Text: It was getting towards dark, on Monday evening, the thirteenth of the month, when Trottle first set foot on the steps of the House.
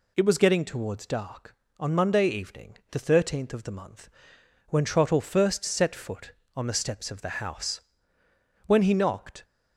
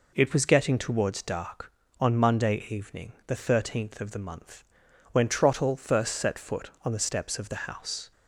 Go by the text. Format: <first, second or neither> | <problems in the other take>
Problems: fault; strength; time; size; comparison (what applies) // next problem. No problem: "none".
second | goes on to say "When he knocked"; noticeable; from 8.6 s on; 0.78 s long